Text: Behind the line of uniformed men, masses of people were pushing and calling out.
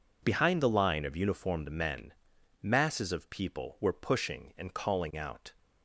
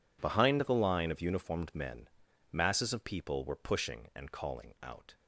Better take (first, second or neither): neither